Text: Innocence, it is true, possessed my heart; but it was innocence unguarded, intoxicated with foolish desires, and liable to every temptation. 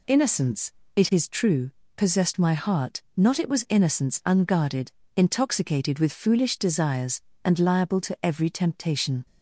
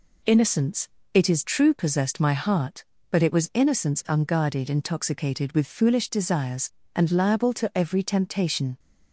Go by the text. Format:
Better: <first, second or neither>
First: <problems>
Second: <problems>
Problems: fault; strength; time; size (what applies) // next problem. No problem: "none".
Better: second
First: says "not" for "but"; at 3.1 s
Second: none